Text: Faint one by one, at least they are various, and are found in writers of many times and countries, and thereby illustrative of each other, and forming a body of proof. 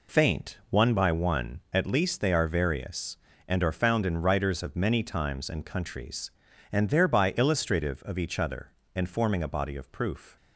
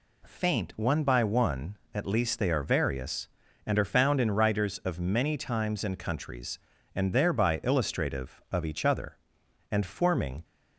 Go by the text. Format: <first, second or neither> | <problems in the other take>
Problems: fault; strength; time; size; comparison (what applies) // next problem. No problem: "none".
first | stops before "a body of proof"; at 10.4 s